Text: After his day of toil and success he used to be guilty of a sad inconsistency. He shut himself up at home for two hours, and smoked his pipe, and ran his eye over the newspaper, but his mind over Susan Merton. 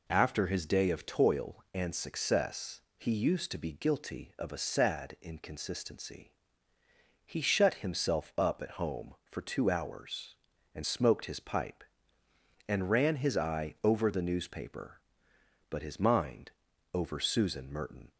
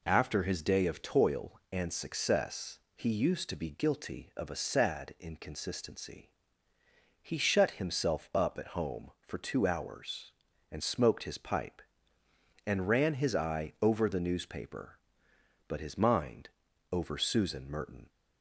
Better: neither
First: pauses between "success" and "he"; slight; at 2.8 s; 0.16 s long // pauses between "mind" and "over"; at 16.5 s; 0.42 s long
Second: pauses between "success" and "he"; slight; at 2.7 s; 0.16 s long // pauses between "mind" and "over"; at 16.4 s; 0.42 s long

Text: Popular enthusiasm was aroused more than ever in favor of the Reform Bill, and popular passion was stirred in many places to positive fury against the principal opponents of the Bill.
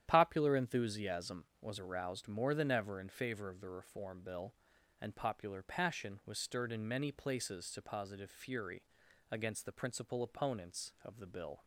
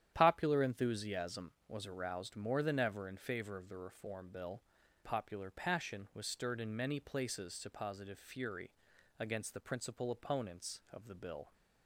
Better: first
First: starts louder than the rest; strong; until 1.0 s; 10.5 dB // pauses between "fury" and "against"; noticeable; at 8.8 s; 0.48 s long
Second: starts louder than the rest; strong; until 1.1 s; 10.5 dB // skips "and"; at 4.8 s // pauses between "fury" and "against"; noticeable; at 8.7 s; 0.48 s long

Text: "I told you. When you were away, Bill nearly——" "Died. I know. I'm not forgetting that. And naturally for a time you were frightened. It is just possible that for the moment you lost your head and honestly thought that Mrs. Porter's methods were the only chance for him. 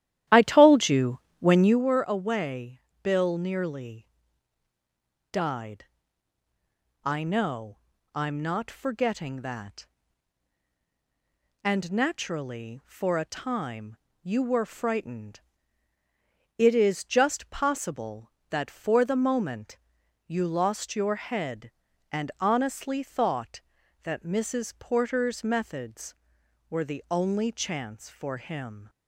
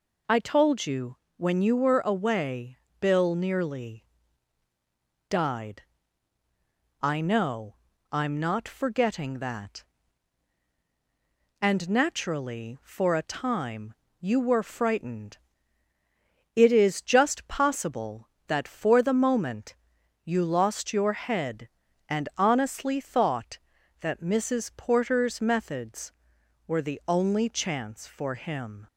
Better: second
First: starts louder than the rest; strong; until 1.9 s; 12.5 dB // pauses between "time" and "you"; slight; at 13.9 s; 0.26 s long // pauses between "moment" and "you"; noticeable; at 19.7 s; 0.48 s long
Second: pauses between "time" and "you"; slight; at 13.9 s; 0.26 s long // pauses between "moment" and "you"; noticeable; at 19.7 s; 0.48 s long

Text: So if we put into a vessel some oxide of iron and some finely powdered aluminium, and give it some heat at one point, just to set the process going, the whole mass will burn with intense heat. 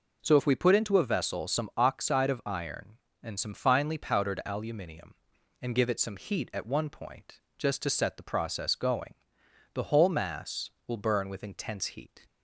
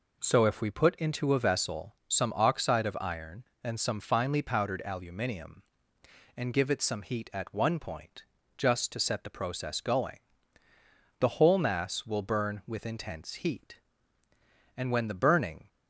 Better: first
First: none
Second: goes on to say "And when the burning"; noticeable; from 14.7 s on; 0.92 s long

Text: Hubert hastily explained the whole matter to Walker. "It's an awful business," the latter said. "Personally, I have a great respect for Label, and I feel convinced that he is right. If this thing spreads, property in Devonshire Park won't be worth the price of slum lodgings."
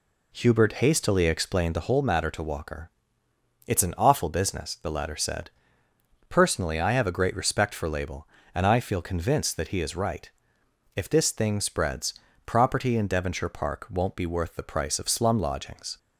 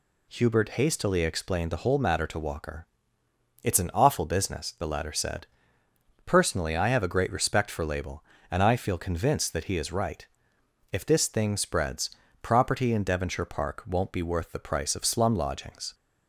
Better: second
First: starts louder than the rest; slight; until 2.0 s; 2.5 dB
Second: none

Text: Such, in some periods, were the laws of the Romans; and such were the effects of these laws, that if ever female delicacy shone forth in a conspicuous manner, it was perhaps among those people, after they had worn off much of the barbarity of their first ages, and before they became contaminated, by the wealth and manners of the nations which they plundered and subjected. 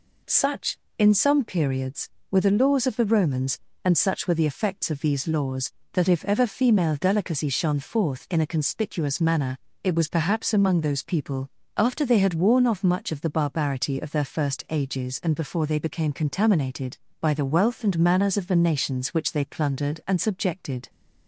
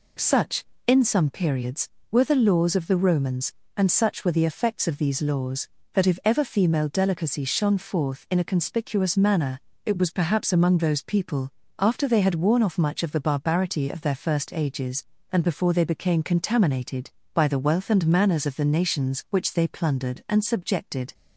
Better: neither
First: none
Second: none

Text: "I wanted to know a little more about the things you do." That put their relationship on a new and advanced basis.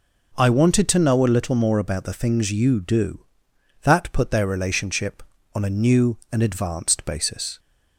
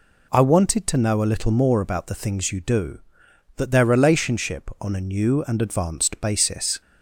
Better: first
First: none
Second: skips "put"; at 3.7 s

